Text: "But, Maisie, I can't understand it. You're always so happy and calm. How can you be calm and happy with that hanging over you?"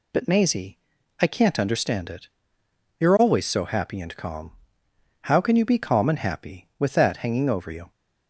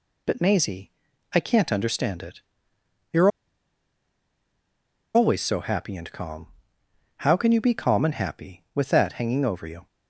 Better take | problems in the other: first | pauses between "You're" and "always"; strong; at 3.3 s; 1.8 s long

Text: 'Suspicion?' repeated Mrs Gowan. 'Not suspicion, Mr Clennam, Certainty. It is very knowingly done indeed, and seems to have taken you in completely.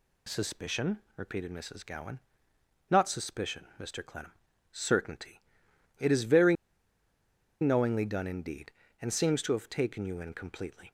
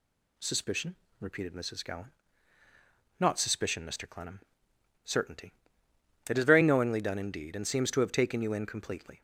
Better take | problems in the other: second | pauses between "very" and "knowingly"; at 6.5 s; 1.0 s long

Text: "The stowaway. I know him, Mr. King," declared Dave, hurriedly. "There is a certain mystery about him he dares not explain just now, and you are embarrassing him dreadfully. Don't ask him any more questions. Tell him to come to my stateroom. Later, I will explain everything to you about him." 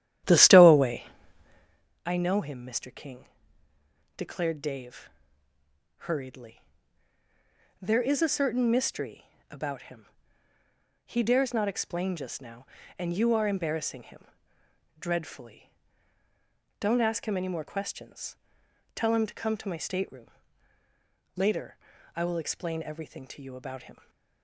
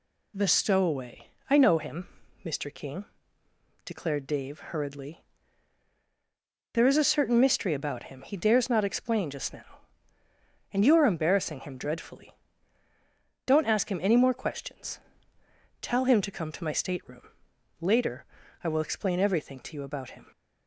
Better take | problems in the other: second | starts louder than the rest; strong; until 1.9 s; 11.5 dB // pauses between "mystery" and "about"; slight; at 9.2 s; 0.24 s long // pauses between "him" and "he"; at 10.0 s; 1.0 s long // pauses between "him" and "dreadfully"; noticeable; at 14.2 s; 0.72 s long

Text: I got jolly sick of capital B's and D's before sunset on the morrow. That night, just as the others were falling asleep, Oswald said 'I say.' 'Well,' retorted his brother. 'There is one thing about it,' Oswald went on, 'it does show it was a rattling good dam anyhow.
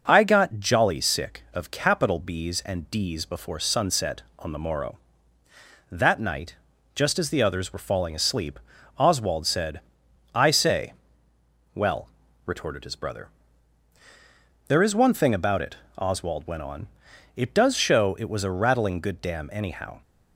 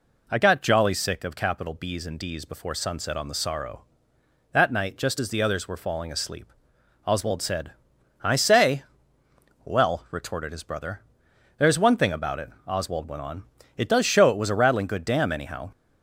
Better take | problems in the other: first | says "sorrow" for "morrow"; at 3.3 s // pauses between "said" and "I"; noticeable; at 7.7 s; 0.50 s long; noticeable in the first

